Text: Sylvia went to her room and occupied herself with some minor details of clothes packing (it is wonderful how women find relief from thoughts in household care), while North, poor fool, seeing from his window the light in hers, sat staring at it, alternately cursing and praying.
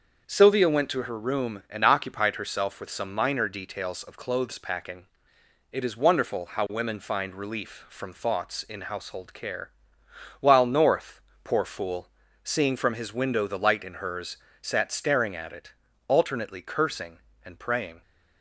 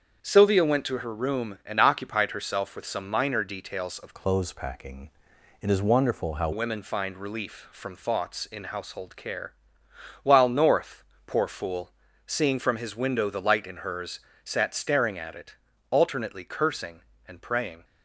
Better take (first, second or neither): first